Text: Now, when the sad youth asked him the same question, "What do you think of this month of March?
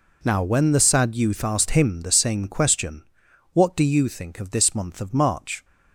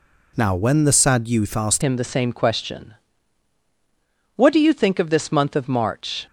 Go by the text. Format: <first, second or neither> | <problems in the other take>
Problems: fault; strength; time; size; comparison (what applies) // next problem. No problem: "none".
first | changes voice at "him"; from 1.8 s on; 4.4 s long